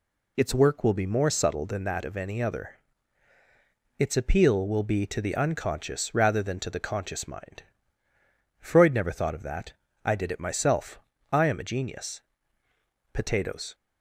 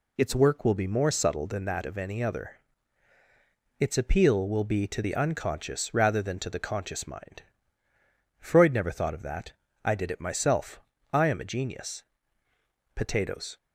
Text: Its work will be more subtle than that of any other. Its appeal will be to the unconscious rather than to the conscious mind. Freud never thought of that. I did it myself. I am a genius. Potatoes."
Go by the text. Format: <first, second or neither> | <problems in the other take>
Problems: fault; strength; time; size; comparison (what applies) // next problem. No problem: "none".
neither | none